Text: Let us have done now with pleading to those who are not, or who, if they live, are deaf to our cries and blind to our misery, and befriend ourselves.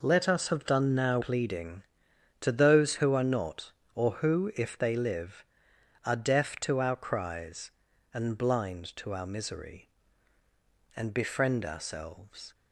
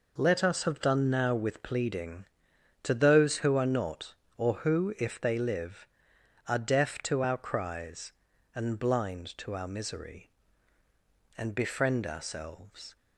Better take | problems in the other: second | skips "with"; at 1.1 s

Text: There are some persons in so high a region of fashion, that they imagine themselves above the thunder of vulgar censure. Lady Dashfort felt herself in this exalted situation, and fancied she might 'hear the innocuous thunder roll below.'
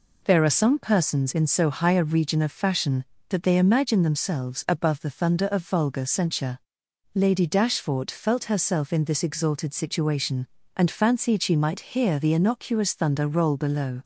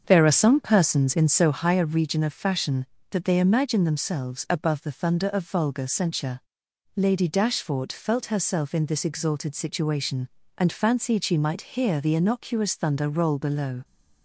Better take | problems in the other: first | starts louder than the rest; strong; until 1.6 s; 7 dB

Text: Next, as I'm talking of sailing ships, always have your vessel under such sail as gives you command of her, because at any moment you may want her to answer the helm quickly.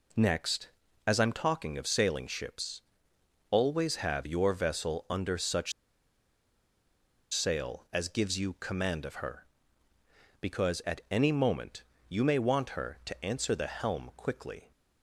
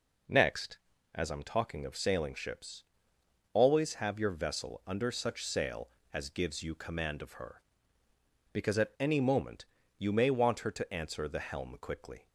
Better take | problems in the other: second | pauses between "such" and "sail"; strong; at 5.7 s; 1.6 s long // pauses between "moment" and "you"; slight; at 11.8 s; 0.26 s long; slight in the second

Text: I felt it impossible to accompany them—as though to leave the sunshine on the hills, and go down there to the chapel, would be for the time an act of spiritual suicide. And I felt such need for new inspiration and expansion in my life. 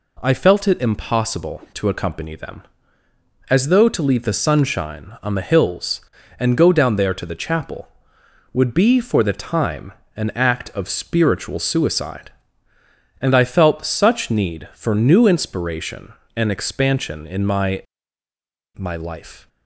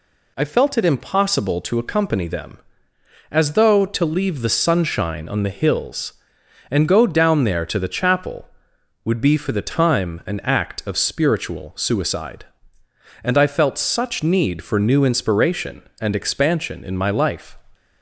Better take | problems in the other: second | pauses between "time" and "an"; slight; at 9.9 s; 0.24 s long // says "my" twice; at 18.7 s

